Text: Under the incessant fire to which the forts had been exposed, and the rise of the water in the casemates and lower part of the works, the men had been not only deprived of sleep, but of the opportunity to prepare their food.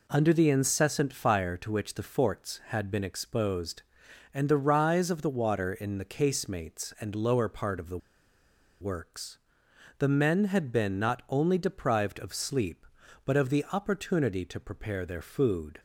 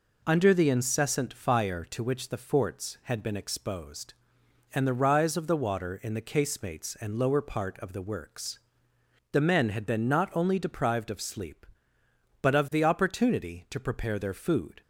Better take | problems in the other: second | pauses between "the" and "works"; noticeable; at 7.9 s; 0.83 s long

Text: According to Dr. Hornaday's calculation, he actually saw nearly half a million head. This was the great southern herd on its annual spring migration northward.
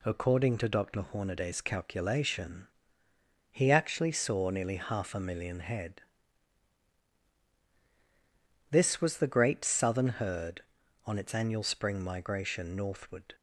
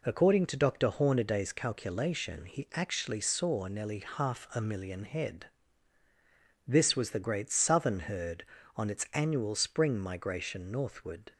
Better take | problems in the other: neither | none

